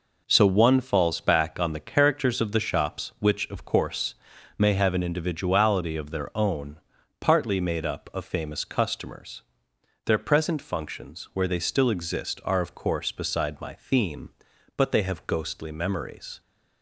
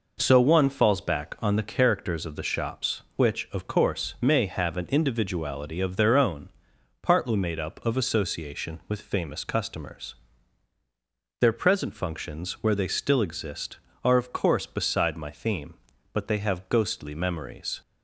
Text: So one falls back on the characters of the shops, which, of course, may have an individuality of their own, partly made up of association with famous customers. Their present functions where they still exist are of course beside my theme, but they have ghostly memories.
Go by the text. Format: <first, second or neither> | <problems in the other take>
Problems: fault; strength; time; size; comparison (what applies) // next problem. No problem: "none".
second | skips "association with"; at 8.2 s